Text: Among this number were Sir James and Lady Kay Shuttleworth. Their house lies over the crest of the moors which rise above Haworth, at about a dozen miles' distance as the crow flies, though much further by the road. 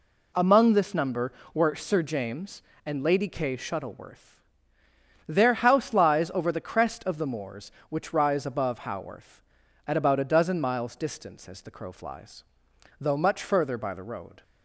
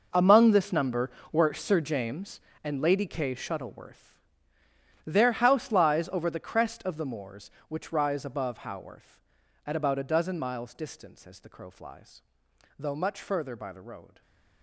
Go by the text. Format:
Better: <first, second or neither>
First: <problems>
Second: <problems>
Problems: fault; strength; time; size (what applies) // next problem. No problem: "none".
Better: first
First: none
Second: gets quieter; strong; throughout; 14.5 dB